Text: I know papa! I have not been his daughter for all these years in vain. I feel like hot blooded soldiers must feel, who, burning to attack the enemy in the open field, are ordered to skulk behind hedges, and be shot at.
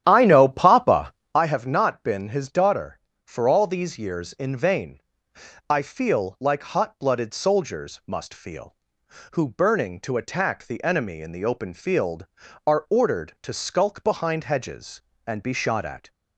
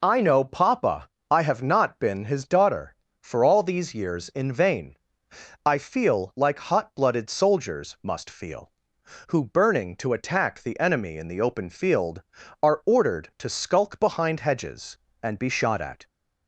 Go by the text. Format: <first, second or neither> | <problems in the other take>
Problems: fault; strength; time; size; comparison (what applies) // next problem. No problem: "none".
second | starts louder than the rest; strong; until 1.4 s; 10.5 dB